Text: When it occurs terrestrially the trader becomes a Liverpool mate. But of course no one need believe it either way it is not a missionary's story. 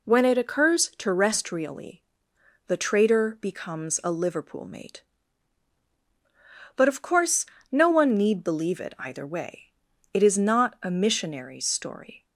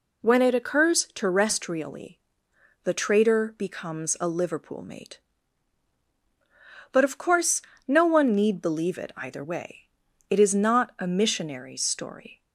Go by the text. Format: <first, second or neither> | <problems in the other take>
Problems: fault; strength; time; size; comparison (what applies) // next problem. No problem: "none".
neither | pauses between "terrestrially" and "the"; noticeable; the same in both // pauses between "course" and "no"; slight; the same in both // pauses between "way" and "it"; the same in both